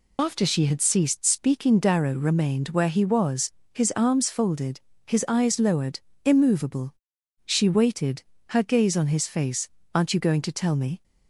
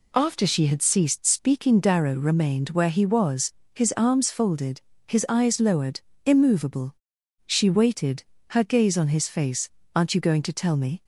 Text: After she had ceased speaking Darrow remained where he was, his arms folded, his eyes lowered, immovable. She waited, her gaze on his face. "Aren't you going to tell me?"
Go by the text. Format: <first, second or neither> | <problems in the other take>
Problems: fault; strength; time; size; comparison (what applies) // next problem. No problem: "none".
second | loses the start of "After"; at 0.1 s; 60 ms